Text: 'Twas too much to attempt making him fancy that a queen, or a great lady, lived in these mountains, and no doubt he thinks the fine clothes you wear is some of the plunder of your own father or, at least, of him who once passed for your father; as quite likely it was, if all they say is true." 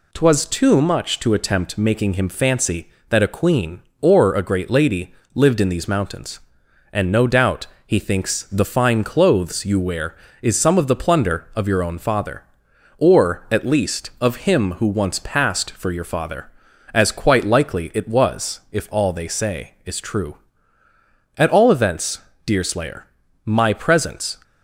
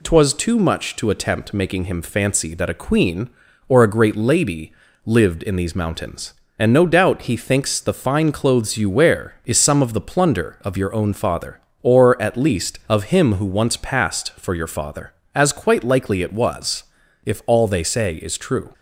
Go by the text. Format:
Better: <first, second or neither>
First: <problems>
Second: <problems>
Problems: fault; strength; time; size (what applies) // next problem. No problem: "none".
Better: second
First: pauses between "doubt" and "he"; slight; at 7.6 s; 0.20 s long // goes on to say "At all events Deerslayer my presence"; strong; from 21.3 s on; 3.0 s long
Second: none